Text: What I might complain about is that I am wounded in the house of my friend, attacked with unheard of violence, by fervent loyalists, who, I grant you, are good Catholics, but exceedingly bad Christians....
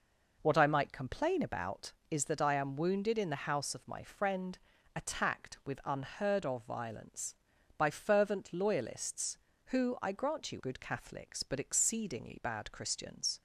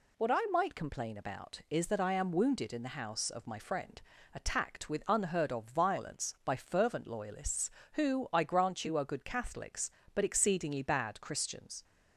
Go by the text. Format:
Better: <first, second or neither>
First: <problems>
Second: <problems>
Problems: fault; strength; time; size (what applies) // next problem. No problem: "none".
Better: second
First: skips "are"; at 10.5 s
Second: none